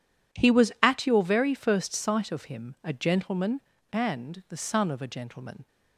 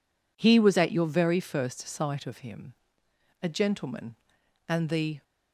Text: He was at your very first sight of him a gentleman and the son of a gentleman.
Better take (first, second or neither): first